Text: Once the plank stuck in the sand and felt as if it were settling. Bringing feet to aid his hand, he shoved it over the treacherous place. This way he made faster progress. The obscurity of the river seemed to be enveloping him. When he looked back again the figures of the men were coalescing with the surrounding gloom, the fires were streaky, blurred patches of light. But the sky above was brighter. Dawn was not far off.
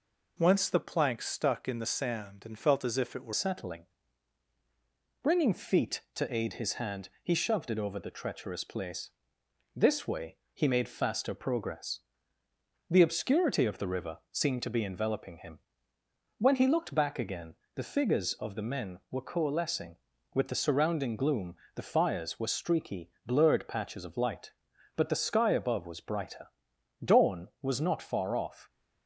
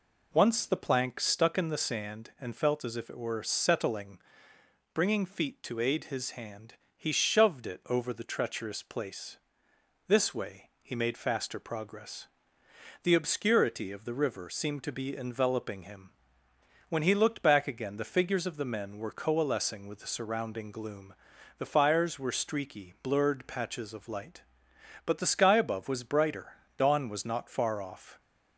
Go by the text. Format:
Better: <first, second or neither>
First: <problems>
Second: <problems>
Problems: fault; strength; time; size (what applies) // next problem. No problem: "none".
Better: second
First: changes voice at "settling"; from 3.3 s on; 25.3 s long // pauses between "way" and "he"; slight; at 10.3 s; 0.16 s long // pauses between "again" and "the"; slight; at 17.5 s; 0.20 s long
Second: none